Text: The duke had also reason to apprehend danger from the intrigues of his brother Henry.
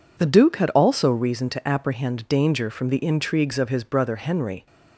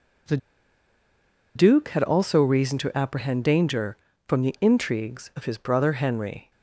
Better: first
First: none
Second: pauses between "The" and "duke"; at 0.3 s; 1.1 s long

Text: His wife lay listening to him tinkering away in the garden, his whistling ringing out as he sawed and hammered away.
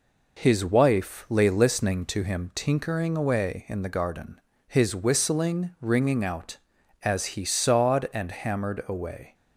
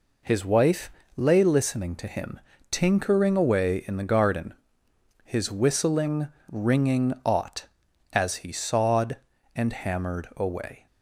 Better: first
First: none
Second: pauses between "wife" and "lay"; slight; at 0.9 s; 0.28 s long // pauses between "him" and "tinkering"; slight; at 2.4 s; 0.30 s long // pauses between "whistling" and "ringing"; slight; at 6.2 s; 0.22 s long // says "ought" for "out"; at 7.2 s

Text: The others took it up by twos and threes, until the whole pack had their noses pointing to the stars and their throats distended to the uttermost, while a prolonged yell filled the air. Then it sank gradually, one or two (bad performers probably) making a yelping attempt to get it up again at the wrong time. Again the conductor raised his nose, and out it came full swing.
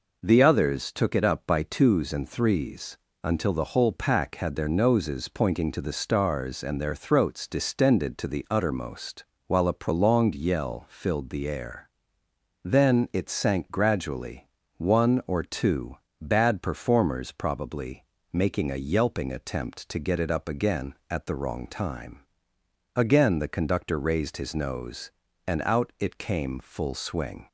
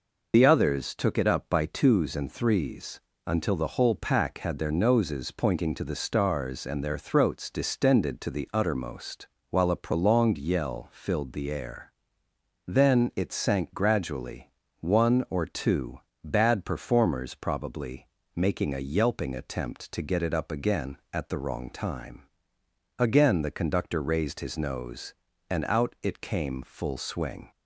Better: first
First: none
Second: loses the start of "The"; at 0.3 s; 95 ms

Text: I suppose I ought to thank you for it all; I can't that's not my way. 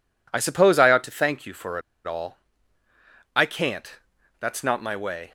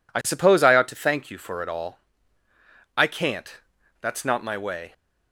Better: second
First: pauses between "for" and "it"; slight; at 1.7 s; 0.26 s long // pauses between "can't" and "that's"; at 3.9 s; 0.44 s long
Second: pauses between "can't" and "that's"; at 3.5 s; 0.44 s long

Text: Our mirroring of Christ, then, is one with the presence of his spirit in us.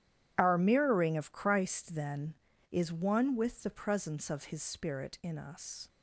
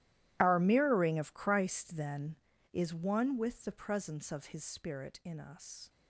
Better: first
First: starts louder than the rest; strong; until 1.3 s; 11.5 dB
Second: gets quieter; strong; throughout; 19.5 dB // starts louder than the rest; strong; until 1.4 s; 14 dB

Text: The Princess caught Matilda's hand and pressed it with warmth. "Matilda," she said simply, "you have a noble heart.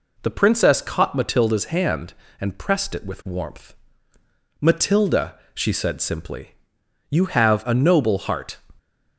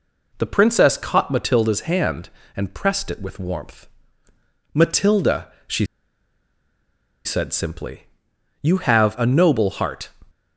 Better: first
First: none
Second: pauses between "she" and "said"; strong; at 5.8 s; 1.3 s long

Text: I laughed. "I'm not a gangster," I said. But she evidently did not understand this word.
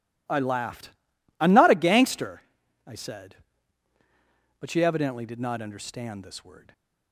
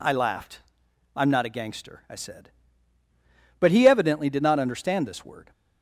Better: first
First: none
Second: says "he" for "she"; at 3.7 s

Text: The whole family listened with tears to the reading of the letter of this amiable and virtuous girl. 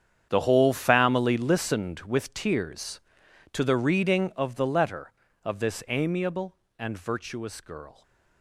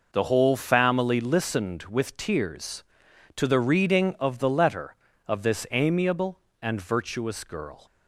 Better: second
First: gets quieter; strong; throughout; 15 dB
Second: none

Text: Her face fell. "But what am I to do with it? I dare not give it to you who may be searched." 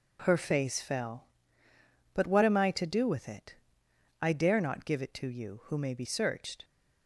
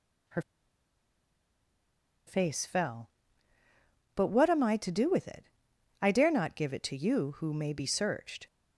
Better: first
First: none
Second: pauses between "Her" and "face"; strong; at 0.4 s; 1.8 s long

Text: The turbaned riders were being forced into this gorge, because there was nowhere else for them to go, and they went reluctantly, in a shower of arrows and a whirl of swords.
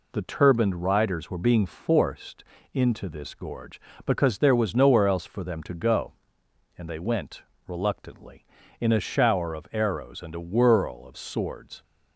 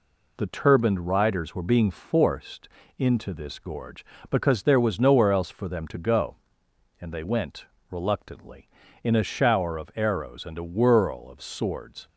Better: neither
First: pauses between "forced" and "into"; slight; at 2.4 s; 0.30 s long // pauses between "went" and "reluctantly"; slight; at 7.4 s; 0.24 s long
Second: pauses between "forced" and "into"; slight; at 2.6 s; 0.30 s long // pauses between "went" and "reluctantly"; slight; at 7.6 s; 0.24 s long

